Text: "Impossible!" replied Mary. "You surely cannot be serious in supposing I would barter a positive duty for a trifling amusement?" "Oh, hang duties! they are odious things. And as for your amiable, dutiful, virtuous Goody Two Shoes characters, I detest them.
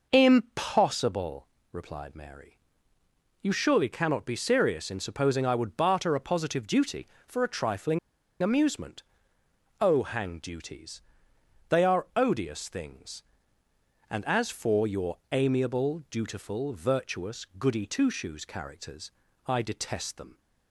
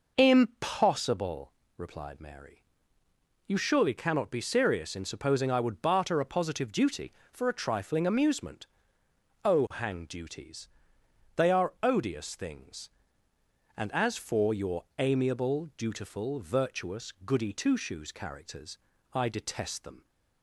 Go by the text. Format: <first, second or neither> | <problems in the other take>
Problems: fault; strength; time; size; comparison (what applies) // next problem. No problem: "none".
second | pauses between "trifling" and "amusement"; at 7.9 s; 0.43 s long // pauses between "virtuous" and "Goody"; slight; at 17.4 s; 0.16 s long; slight in the second